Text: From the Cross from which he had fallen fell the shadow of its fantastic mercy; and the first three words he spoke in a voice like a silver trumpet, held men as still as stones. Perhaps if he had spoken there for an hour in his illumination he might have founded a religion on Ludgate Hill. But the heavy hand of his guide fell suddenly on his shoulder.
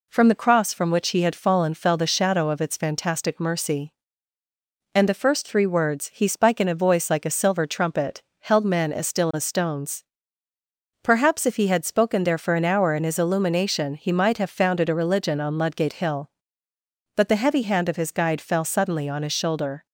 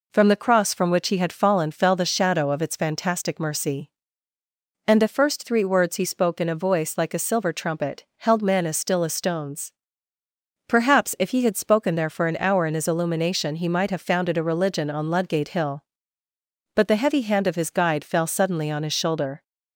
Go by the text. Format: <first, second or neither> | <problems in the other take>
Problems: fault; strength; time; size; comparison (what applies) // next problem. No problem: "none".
second | says "spike" for "spoke"; at 6.2 s